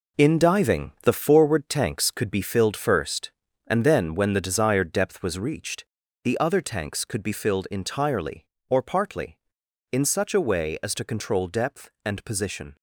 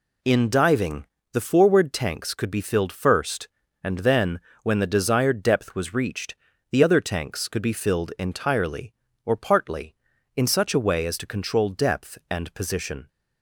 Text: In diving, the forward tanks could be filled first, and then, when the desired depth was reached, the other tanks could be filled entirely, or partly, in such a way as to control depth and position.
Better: second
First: gets quieter; strong; throughout; 7.5 dB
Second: none

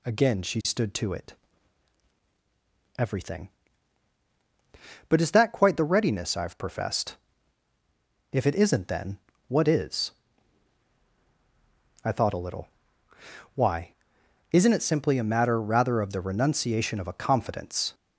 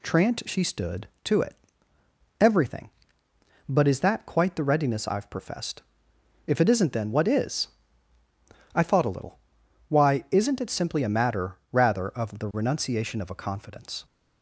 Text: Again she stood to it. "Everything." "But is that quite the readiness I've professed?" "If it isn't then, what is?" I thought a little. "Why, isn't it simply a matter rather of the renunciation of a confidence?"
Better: first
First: none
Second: says "Trant" for "Again"; at 0.0 s

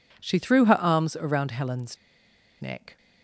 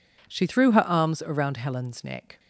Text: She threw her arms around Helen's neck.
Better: second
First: pauses between "Helen's" and "neck"; noticeable; at 1.9 s; 0.63 s long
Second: none

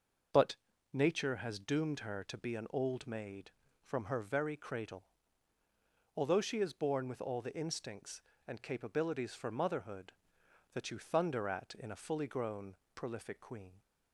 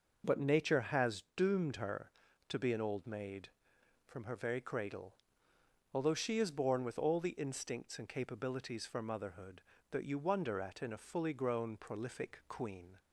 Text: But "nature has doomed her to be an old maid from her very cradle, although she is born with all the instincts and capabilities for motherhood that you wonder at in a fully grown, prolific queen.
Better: second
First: pauses between "But" and "nature"; slight; at 0.5 s; 0.36 s long // says "thunder" for "wonder"; at 10.9 s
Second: none

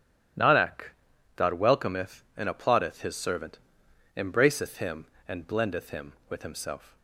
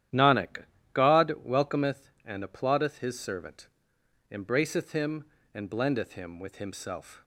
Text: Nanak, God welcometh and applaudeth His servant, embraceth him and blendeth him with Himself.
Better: neither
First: starts louder than the rest; strong; until 1.8 s; 12 dB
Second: starts louder than the rest; strong; until 1.5 s; 11.5 dB

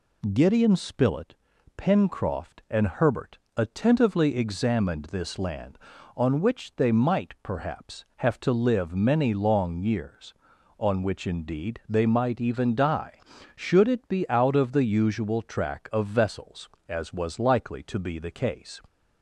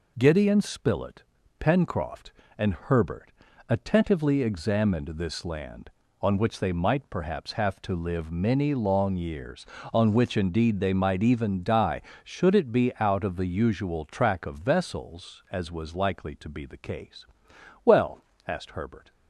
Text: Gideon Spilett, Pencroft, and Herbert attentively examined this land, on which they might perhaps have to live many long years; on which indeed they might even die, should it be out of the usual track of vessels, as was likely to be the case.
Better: first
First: pauses between "Herbert" and "attentively"; slight; at 3.3 s; 0.18 s long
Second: pauses between "Herbert" and "attentively"; slight; at 3.3 s; 0.34 s long // goes on to say "Well asked Herbert"; noticeable; from 17.8 s on; 1.2 s long

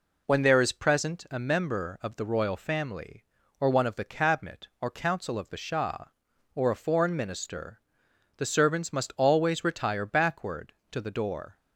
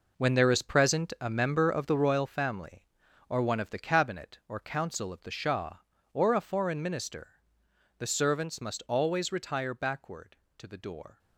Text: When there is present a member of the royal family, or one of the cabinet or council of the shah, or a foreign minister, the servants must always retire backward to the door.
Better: first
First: none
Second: gets quieter; strong; throughout; 11 dB

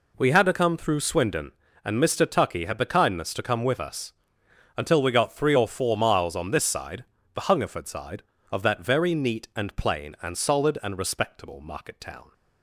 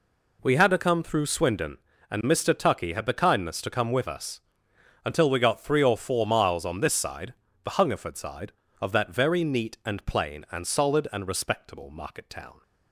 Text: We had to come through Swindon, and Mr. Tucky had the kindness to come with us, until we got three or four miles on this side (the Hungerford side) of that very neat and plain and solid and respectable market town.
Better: neither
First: none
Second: none

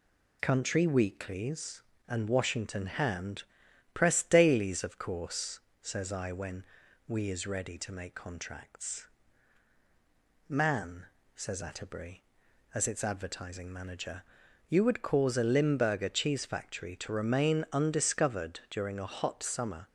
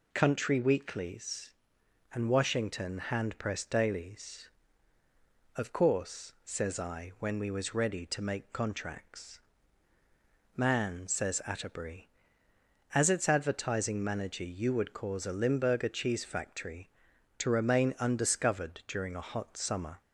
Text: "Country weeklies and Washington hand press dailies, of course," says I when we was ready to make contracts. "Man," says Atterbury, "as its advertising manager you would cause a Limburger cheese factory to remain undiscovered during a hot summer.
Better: second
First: pauses between "hand" and "press"; noticeable; at 3.4 s; 0.50 s long // pauses between "when" and "we"; noticeable; at 6.6 s; 0.46 s long // says "is" for "was"; at 7.2 s // pauses between "manager" and "you"; noticeable; at 14.2 s; 0.46 s long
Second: none

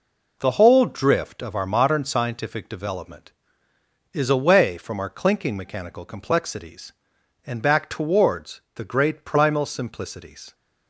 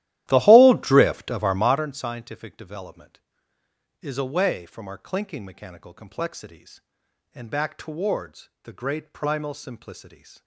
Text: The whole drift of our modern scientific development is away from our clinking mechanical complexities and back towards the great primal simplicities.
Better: first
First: none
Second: starts louder than the rest; strong; until 1.9 s; 14 dB

